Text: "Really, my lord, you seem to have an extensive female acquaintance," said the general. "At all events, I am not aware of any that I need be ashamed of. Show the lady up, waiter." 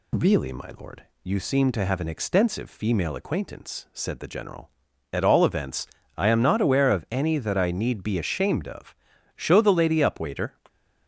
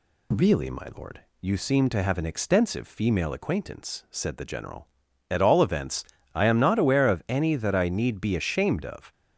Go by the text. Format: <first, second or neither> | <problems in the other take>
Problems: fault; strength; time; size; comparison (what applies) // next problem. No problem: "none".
first | stops before "Show the lady up waiter"; at 9.1 s